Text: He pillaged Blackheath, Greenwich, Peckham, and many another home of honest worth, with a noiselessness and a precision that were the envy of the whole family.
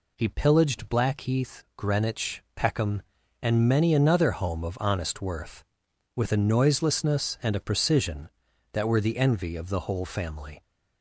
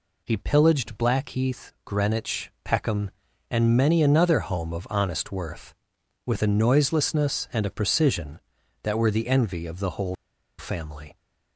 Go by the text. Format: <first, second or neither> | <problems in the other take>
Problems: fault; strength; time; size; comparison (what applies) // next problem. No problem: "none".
first | pauses between "whole" and "family"; at 10.1 s; 0.43 s long